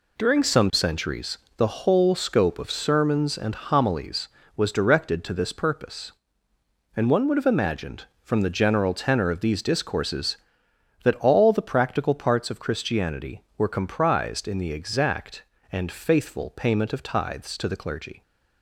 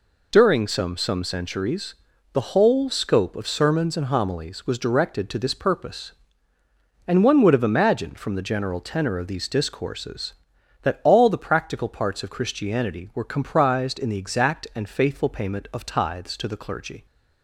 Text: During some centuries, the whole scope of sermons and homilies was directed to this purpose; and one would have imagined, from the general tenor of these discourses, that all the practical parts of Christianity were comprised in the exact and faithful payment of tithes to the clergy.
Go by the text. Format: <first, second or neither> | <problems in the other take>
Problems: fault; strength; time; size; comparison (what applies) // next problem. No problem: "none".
first | says "some" twice; at 0.9 s